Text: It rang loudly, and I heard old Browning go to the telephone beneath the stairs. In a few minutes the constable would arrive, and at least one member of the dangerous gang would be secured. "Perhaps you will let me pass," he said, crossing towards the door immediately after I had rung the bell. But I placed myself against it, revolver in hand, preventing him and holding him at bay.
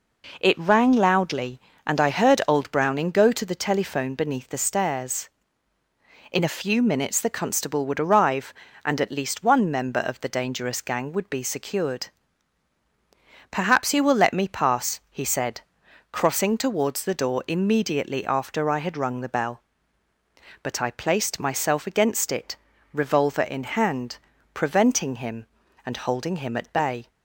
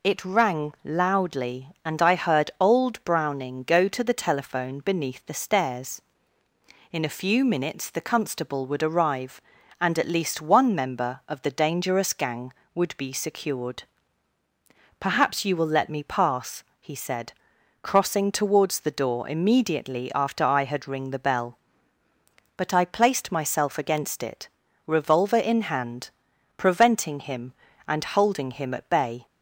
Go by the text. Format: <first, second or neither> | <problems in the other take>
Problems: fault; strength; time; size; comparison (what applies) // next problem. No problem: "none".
first | says "ring" for "rung"; at 20.8 s